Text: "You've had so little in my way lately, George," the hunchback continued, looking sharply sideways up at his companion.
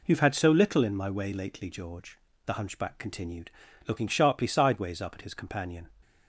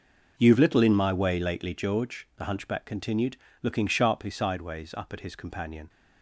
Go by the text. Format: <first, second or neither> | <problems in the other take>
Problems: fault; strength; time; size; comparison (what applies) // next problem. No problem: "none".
first | skips "had so"; at 0.5 s